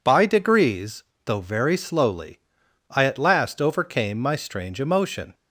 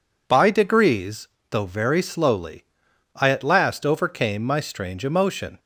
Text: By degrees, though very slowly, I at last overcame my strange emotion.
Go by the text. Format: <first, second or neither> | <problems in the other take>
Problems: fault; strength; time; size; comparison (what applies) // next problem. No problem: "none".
neither | none